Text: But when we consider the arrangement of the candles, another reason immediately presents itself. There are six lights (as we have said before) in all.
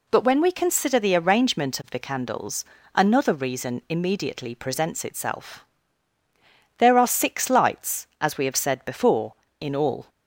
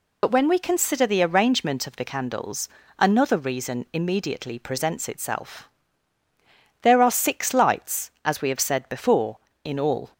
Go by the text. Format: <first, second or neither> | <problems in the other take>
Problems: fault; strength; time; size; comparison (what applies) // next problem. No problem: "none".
first | loses the start of "But"; at 0.2 s; 65 ms